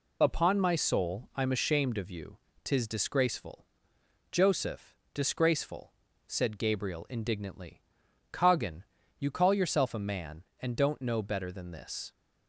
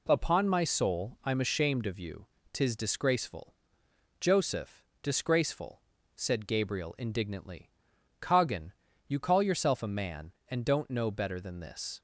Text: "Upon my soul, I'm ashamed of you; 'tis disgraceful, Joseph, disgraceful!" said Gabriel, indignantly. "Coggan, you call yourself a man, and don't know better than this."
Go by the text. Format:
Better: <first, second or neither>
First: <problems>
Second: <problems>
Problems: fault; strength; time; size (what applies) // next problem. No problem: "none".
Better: second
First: loses the start of "Upon"; at 0.2 s; 30 ms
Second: none